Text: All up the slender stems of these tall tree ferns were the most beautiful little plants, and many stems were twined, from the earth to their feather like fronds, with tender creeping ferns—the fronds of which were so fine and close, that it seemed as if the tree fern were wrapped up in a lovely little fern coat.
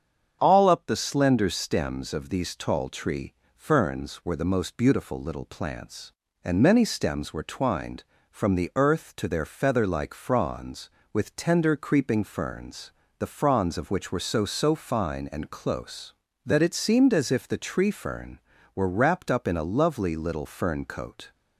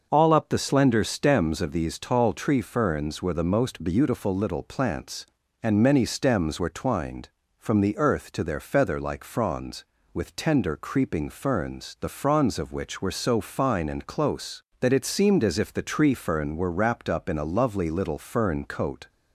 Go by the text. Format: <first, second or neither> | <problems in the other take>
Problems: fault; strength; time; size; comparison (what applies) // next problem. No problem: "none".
second | starts louder than the rest; strong; until 1.4 s; 7.5 dB; noticeable in the second // pauses between "tree" and "ferns"; slight; at 3.3 s; 0.24 s long // says "so" twice; at 14.4 s